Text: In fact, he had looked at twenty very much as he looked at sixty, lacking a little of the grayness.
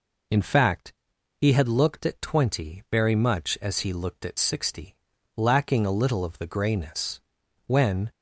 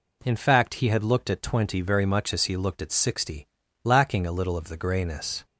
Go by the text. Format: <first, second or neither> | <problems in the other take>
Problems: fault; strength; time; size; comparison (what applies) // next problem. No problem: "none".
second | goes on to say "When"; slight; from 7.6 s on; 0.44 s long